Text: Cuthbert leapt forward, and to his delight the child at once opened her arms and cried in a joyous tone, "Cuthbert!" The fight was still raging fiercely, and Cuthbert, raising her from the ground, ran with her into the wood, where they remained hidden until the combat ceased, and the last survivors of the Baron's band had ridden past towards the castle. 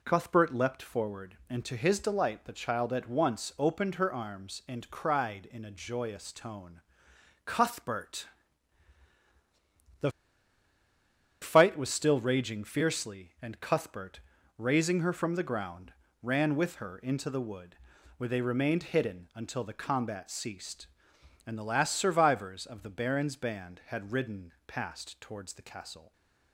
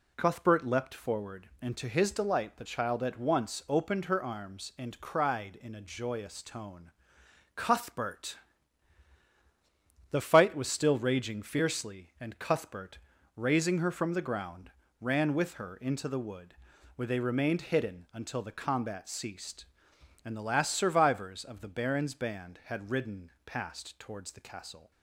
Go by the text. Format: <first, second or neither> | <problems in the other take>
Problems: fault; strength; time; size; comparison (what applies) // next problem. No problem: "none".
second | pauses between "The" and "fight"; strong; at 10.0 s; 1.3 s long // stays silent after the last word; slight; from 26.0 s on; 0.5 s long